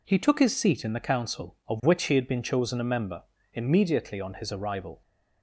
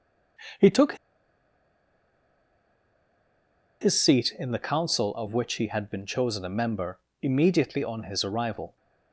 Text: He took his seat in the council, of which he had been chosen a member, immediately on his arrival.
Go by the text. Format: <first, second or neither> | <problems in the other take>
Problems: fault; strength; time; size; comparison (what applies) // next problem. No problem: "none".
first | pauses between "took" and "his"; strong; at 0.9 s; 2.8 s long